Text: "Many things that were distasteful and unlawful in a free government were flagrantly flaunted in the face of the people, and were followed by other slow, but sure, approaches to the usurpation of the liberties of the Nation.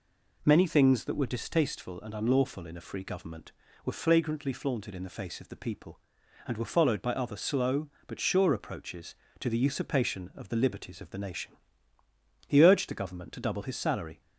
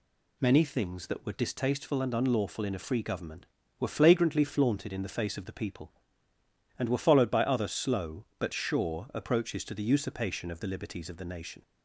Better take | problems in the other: second | goes on to say "He urged the Government to double his salary"; strong; from 12.4 s on; 1.7 s long

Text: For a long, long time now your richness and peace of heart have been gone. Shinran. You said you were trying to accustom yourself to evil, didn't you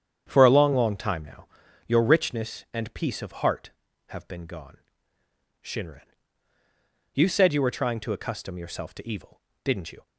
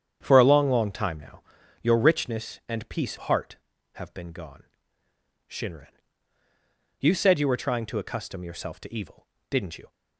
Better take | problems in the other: first | starts louder than the rest; strong; until 1.2 s; 8.5 dB; strong in the first // pauses between "now" and "your"; at 1.3 s; 0.42 s long; also in the first // skips "of"; at 3.1 s

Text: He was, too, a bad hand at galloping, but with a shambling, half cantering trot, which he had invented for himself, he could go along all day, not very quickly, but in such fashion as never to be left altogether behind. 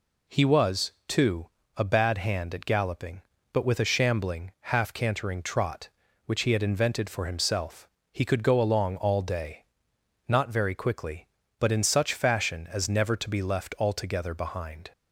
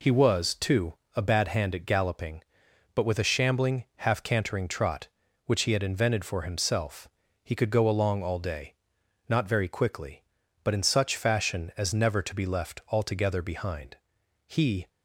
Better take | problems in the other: first | goes on to say "He"; slight; from 14.4 s on; 0.40 s long

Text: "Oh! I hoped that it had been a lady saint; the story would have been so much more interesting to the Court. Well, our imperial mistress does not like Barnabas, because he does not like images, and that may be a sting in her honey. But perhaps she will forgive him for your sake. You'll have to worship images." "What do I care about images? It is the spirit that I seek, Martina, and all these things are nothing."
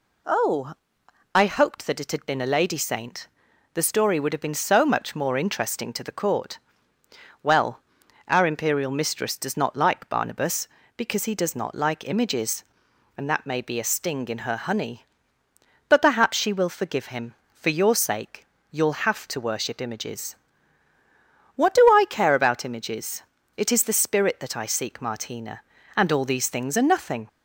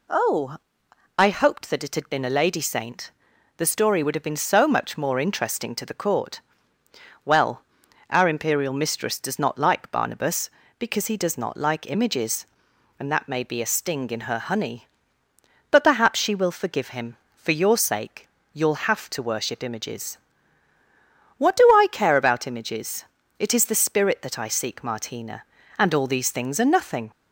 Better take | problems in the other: neither | none

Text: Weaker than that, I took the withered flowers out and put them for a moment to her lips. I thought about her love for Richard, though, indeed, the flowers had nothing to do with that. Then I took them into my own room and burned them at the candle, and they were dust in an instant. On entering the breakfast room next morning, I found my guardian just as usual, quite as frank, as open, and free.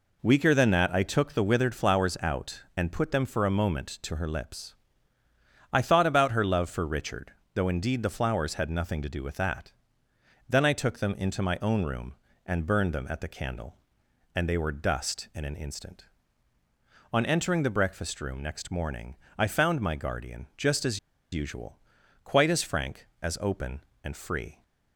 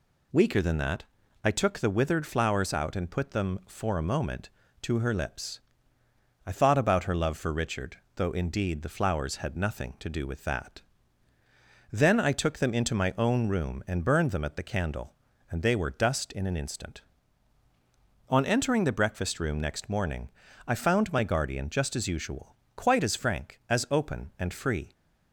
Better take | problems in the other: second | pauses between "as" and "usual"; slight; at 20.9 s; 0.33 s long

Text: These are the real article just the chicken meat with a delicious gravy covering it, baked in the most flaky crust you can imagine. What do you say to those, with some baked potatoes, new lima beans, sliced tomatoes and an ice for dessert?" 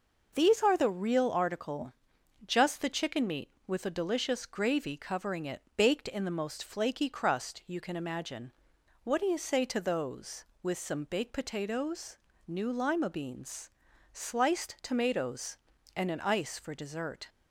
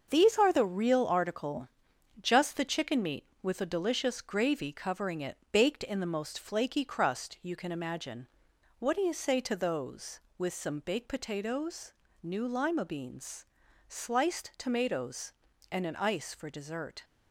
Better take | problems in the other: first | gets quieter; throughout; 6.5 dB // pauses between "article" and "just"; noticeable; at 1.6 s; 0.54 s long; noticeable in the first

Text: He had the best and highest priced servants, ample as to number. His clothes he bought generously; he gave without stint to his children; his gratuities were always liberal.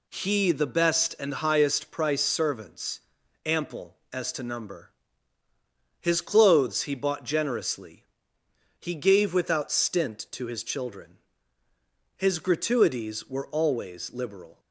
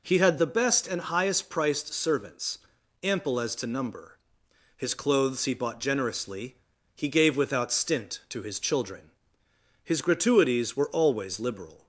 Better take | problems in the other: second | skips "had"; at 0.5 s

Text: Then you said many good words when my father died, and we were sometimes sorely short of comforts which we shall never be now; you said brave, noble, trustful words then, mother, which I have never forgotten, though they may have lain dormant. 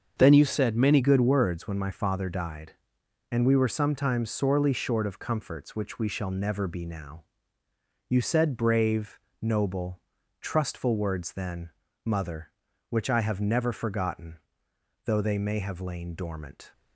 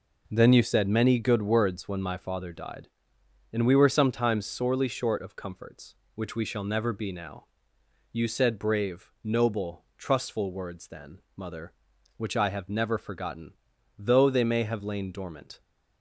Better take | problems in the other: second | starts louder than the rest; until 1.1 s; 6.5 dB // changes voice at "good"; from 1.0 s on; 15.7 s long

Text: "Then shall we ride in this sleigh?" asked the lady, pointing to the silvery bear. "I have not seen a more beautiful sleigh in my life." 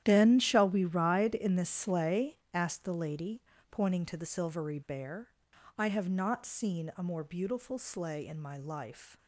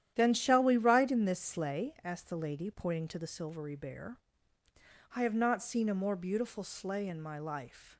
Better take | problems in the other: second | gets quieter; strong; throughout; 13.5 dB // starts louder than the rest; strong; until 1.0 s; 11 dB; strong in the second

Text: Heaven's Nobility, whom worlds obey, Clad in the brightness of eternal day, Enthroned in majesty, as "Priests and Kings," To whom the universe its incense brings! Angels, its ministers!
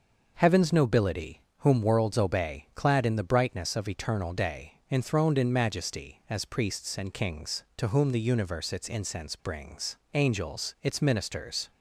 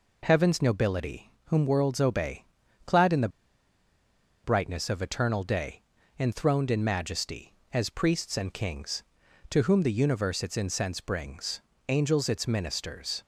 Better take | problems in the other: first | pauses between "the" and "brightness"; at 3.2 s; 1.1 s long

